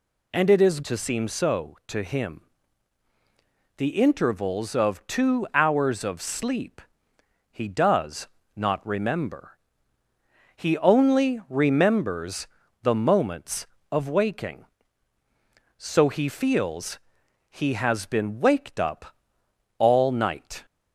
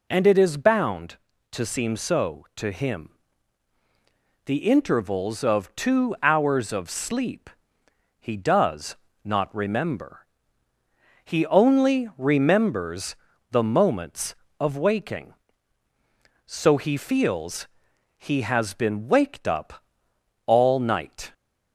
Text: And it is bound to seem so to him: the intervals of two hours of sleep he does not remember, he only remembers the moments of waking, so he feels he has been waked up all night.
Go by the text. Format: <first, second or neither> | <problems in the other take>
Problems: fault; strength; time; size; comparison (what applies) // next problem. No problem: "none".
second | skips "bound"; at 0.8 s // pauses between "sleep" and "he"; noticeable; at 6.8 s; 0.68 s long; noticeable in the second // pauses between "does" and "not"; slight; at 8.2 s; 0.30 s long; slight in the second // pauses between "remembers" and "the"; slight; at 12.4 s; 0.36 s long; slight in the second // pauses between "feels" and "he"; noticeable; at 16.9 s; 0.50 s long; noticeable in the second // pauses between "up" and "all"; noticeable; at 19.1 s; 0.62 s long; noticeable in the second